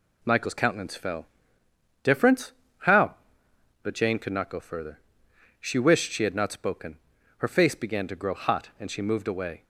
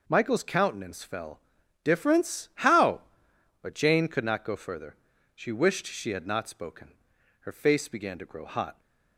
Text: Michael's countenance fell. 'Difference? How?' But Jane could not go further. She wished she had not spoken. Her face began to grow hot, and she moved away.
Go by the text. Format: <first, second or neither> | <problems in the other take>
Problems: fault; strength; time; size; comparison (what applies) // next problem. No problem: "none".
first | stops before "and she moved away"; at 8.7 s